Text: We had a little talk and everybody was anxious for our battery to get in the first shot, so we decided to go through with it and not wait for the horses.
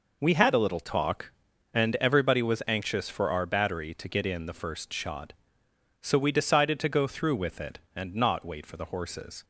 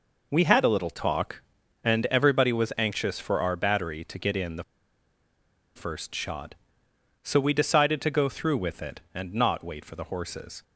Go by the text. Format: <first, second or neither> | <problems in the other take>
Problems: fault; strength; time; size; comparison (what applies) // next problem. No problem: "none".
first | pauses between "the" and "first"; at 4.6 s; 1.1 s long